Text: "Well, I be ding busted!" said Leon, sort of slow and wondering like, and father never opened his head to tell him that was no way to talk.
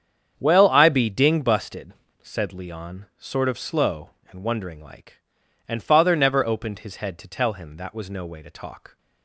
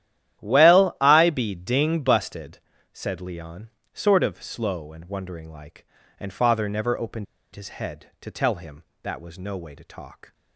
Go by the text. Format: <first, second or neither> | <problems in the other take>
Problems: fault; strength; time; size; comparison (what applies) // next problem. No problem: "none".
first | starts louder than the rest; strong; until 1.4 s; 11.5 dB; strong in the first // pauses between "opened" and "his"; slight; at 7.2 s; 0.29 s long